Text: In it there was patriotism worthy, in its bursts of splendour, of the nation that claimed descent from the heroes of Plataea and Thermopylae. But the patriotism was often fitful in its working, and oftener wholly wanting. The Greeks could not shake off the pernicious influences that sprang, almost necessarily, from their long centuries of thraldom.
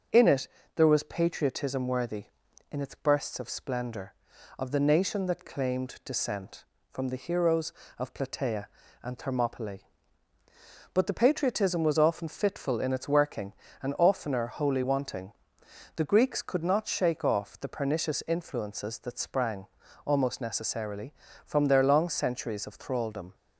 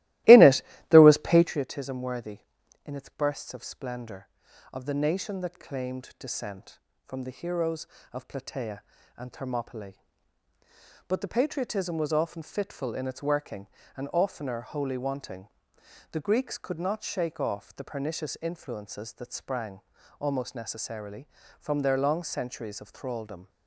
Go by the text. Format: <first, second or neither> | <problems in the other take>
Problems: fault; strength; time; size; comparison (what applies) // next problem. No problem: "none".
first | starts louder than the rest; strong; until 1.6 s; 16.5 dB // pauses between "it" and "there"; slight; at 0.6 s; 0.28 s long; slight in the first